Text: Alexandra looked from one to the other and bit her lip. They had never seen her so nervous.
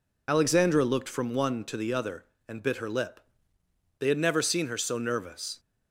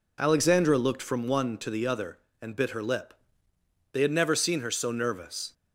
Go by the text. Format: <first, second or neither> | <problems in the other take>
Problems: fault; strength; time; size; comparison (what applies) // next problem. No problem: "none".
second | loses the start of "Alexandra"; at 0.2 s; 35 ms